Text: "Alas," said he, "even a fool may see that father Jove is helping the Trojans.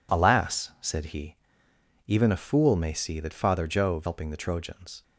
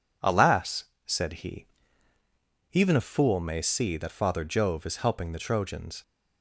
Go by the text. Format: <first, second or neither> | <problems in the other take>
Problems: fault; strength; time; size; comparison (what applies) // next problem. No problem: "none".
second | skips "is"; at 4.0 s